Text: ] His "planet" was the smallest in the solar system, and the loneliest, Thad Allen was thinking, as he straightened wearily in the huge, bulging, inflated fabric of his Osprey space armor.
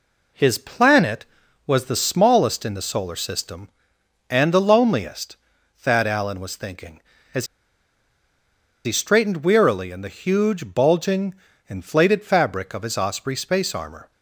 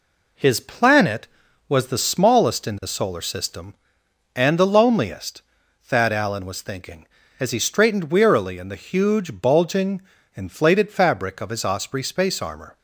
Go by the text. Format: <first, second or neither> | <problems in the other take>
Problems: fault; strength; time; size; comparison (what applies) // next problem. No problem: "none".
second | pauses between "as" and "he"; strong; at 7.4 s; 1.3 s long